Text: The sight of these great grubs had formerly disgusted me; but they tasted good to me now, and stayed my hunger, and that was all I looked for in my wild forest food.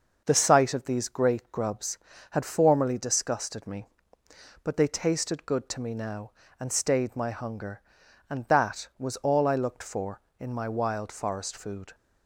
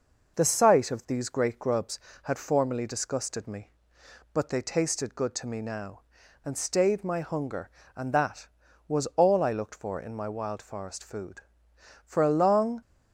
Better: first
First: none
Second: goes on to say "For a long"; noticeable; from 12.0 s on; 0.78 s long

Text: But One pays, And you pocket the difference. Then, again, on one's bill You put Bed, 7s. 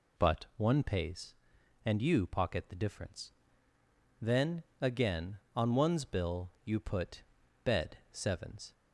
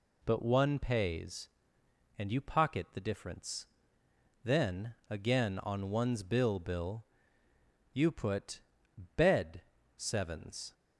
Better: first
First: pauses between "put" and "Bed"; at 7.2 s; 0.44 s long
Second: says "bill" twice; at 6.5 s // pauses between "put" and "Bed"; noticeable; at 8.6 s; 0.56 s long

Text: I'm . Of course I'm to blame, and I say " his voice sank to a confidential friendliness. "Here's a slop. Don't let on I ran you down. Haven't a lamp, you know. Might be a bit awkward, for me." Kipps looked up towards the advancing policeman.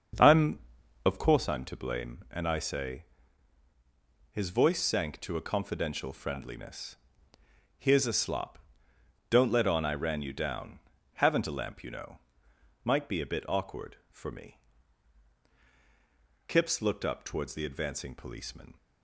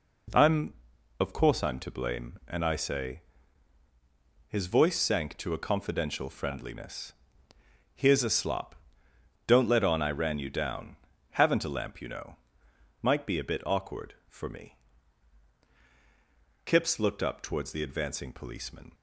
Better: second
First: starts louder than the rest; until 1.4 s; 6.5 dB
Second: none

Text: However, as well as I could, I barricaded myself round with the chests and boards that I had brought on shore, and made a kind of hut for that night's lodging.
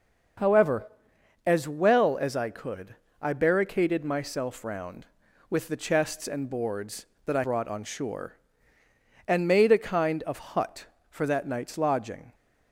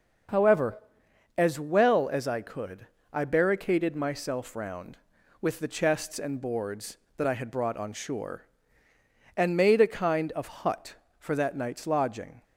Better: second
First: skips "had"; at 7.4 s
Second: none

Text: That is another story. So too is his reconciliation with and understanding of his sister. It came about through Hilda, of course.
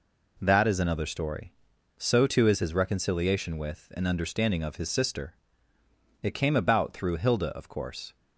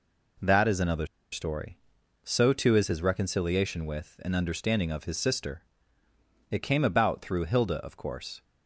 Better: first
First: none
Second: pauses between "another" and "story"; slight; at 1.0 s; 0.25 s long

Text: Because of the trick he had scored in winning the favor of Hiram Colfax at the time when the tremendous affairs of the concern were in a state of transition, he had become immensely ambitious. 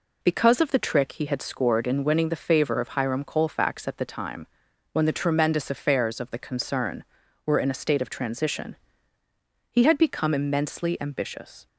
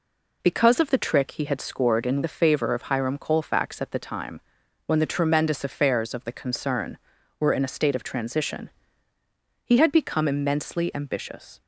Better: first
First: pauses between "time" and "when"; at 4.4 s; 0.44 s long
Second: skips "winning"; at 2.2 s // pauses between "time" and "when"; at 4.4 s; 0.44 s long

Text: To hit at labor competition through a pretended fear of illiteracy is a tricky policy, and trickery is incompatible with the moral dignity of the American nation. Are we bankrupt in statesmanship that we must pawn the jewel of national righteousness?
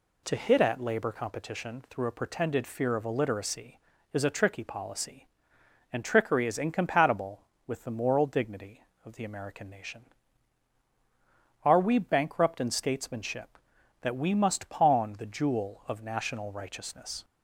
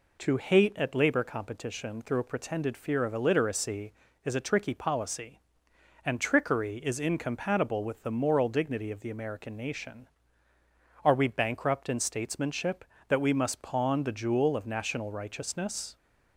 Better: first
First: none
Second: says "hate" for "hit"; at 0.3 s

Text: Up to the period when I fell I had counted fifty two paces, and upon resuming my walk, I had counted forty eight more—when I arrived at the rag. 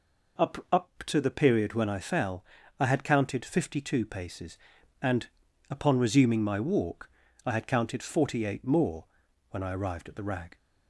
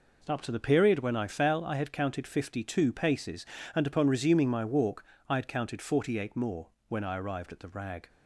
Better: second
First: says "Up" twice; at 0.7 s // pauses between "fell" and "I"; slight; at 2.4 s; 0.34 s long // pauses between "and" and "upon"; at 5.2 s; 0.42 s long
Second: none

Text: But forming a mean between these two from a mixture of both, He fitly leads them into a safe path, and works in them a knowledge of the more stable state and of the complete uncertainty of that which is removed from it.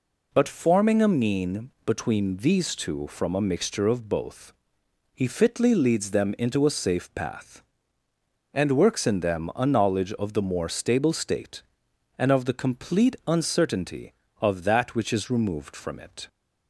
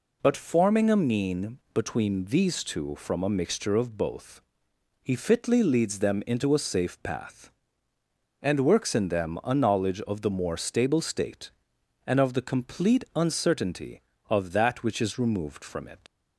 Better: first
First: none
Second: leaves "it" unfinished; at 16.0 s; 95 ms

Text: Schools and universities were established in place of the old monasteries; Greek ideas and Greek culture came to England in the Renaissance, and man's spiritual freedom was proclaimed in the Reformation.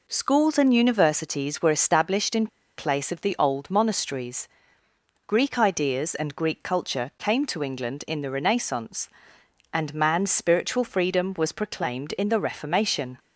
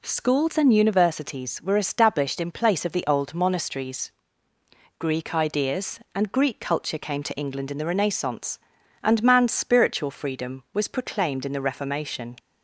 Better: second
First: pauses between "in" and "place"; slight; at 2.4 s; 0.30 s long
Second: none

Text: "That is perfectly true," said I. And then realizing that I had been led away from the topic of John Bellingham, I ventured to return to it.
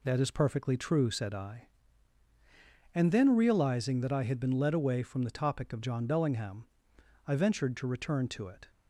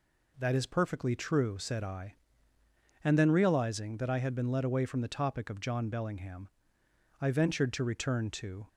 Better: first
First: none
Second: stops before "it"; at 8.6 s

